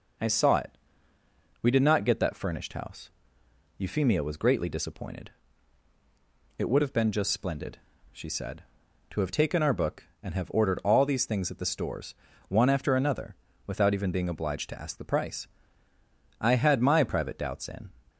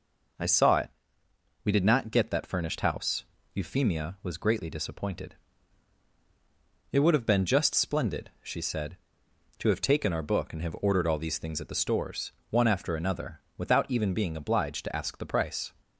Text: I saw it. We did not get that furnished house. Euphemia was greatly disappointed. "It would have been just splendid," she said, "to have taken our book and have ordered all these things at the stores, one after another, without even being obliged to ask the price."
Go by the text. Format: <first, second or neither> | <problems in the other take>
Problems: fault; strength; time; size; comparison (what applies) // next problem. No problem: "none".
second | goes on to say "I had my private doubts in"; from 16.3 s on; 1.5 s long